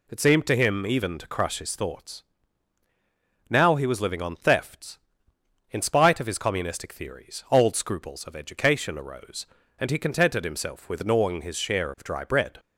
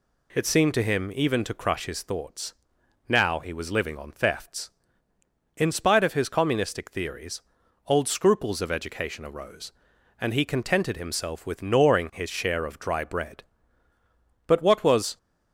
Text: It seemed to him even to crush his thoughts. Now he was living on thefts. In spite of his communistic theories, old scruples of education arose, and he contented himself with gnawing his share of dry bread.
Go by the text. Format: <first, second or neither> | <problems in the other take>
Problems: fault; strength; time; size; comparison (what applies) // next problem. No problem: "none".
first | goes on to say "But what was"; noticeable; from 14.4 s on; 0.70 s long